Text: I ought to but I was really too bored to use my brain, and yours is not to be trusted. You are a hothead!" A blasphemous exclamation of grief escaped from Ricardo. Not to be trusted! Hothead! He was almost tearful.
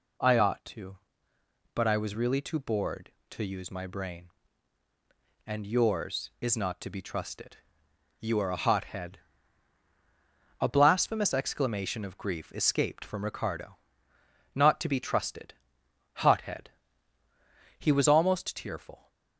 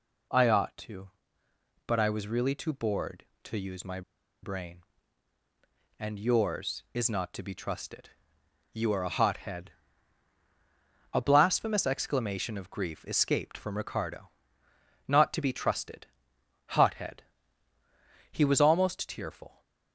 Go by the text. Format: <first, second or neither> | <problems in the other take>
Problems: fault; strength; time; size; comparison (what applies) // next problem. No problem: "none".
first | pauses between "my" and "brain"; at 4.0 s; 0.41 s long